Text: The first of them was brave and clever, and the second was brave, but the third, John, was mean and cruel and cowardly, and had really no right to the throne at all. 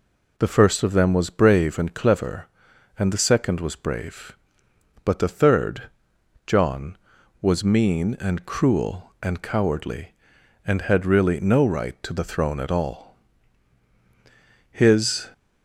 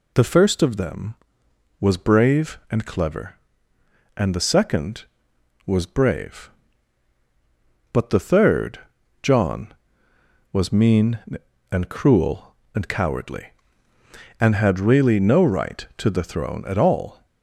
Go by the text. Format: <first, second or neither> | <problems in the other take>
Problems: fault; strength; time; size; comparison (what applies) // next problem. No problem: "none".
second | goes on to say "His"; from 14.7 s on; 0.58 s long